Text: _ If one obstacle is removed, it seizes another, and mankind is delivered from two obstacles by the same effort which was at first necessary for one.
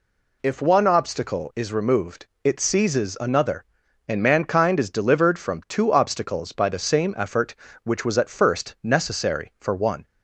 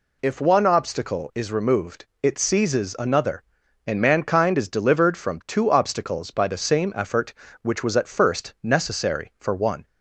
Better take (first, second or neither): neither